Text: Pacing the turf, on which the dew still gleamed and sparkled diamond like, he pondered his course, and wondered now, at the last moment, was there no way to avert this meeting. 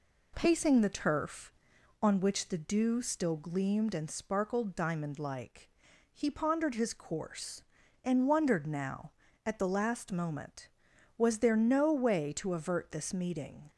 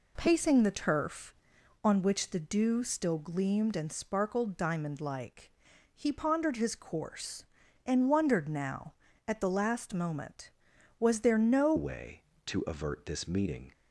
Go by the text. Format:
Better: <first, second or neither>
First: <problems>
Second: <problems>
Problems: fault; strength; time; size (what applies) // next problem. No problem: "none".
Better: first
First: none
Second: changes voice at "way"; from 11.7 s on; 2.0 s long